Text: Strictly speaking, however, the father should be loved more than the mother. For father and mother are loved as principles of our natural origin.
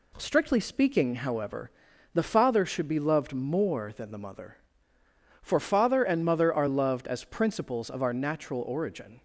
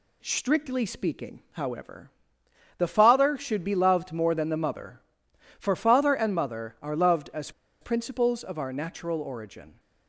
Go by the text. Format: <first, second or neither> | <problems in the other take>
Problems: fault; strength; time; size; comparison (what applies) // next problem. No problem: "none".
first | pauses between "as" and "principles"; slight; at 7.5 s; 0.30 s long